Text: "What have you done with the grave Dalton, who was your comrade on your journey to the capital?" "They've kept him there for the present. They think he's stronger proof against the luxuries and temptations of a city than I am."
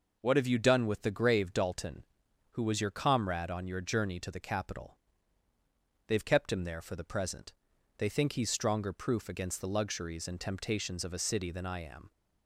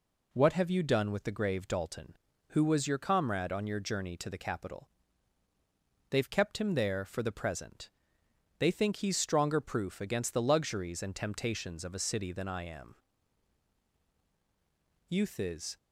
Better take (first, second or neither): first